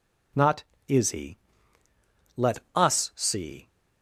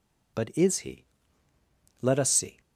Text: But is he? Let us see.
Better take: second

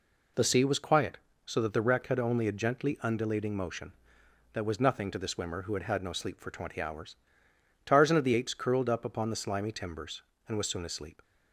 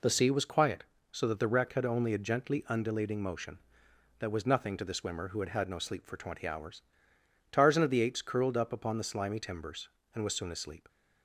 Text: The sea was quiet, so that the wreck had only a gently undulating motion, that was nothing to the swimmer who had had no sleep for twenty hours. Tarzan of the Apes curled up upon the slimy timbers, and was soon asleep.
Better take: neither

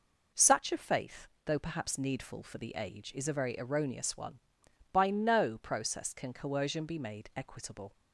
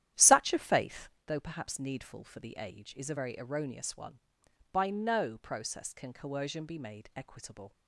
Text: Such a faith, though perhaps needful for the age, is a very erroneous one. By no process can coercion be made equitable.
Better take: first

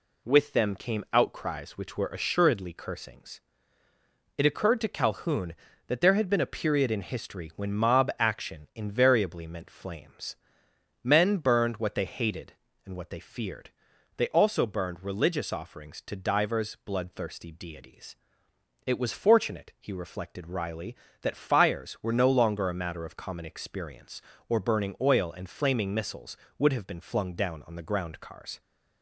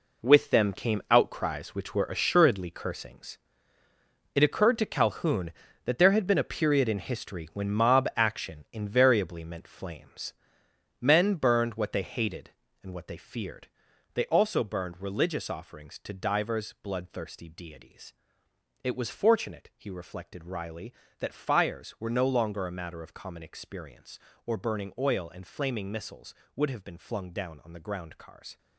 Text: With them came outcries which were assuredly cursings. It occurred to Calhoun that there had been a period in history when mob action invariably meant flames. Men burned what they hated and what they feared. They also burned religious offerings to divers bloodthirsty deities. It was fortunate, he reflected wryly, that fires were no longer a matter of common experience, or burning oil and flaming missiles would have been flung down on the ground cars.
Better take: first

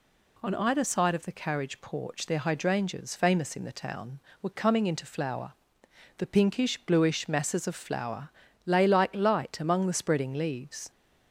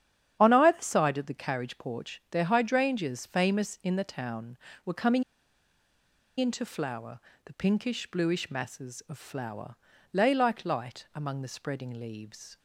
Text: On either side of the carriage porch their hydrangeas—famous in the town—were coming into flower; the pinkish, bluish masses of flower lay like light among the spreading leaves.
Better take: first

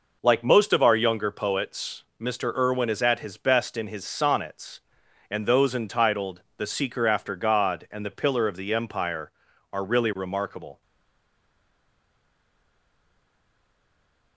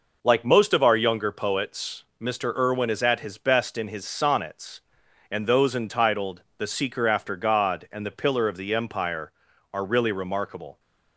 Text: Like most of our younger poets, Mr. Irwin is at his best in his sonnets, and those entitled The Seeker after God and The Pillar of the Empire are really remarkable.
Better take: second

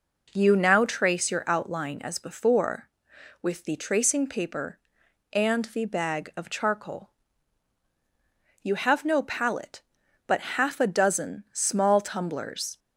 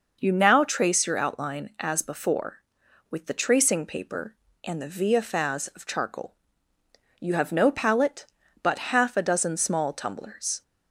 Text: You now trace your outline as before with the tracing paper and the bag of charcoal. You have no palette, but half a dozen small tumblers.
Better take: first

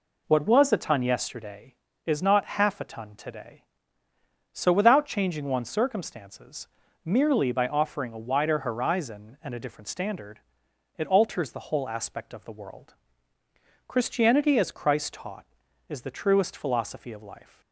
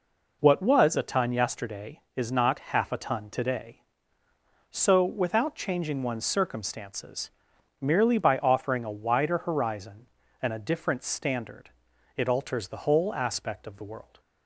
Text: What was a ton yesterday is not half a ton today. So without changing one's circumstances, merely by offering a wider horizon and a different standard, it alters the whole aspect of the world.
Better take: second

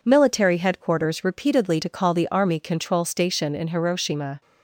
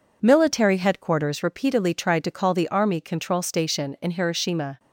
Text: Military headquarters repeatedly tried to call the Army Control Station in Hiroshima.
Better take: second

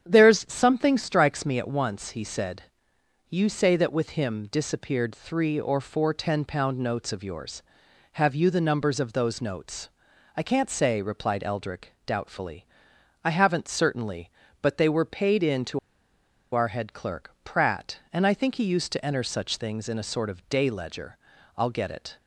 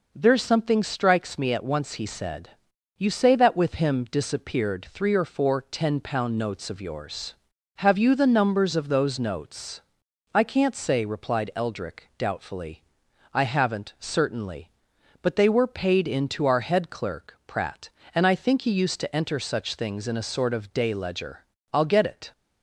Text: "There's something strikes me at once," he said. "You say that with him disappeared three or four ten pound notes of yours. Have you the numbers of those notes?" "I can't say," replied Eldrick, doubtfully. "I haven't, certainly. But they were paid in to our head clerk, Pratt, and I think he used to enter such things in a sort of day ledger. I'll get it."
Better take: second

